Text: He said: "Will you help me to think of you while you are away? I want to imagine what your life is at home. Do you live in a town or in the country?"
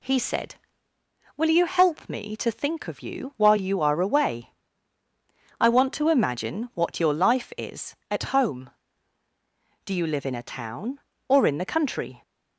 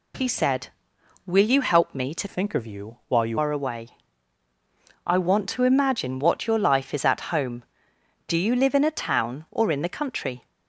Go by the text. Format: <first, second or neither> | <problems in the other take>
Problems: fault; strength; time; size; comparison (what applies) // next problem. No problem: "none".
first | changes voice from "think" to "you"; from 2.2 to 3.3 s; 1.1 s long